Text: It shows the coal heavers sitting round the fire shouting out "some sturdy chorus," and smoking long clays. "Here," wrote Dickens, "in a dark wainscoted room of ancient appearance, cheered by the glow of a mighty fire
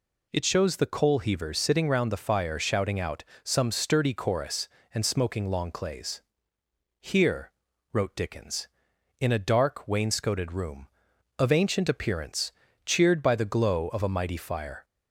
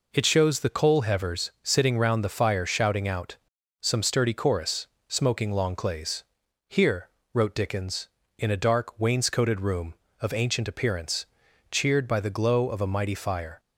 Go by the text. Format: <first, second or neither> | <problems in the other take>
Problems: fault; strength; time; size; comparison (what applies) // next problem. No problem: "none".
first | pauses between "out" and "some"; noticeable; at 3.3 s; 0.46 s long; slight in the first // skips "and"; at 4.9 s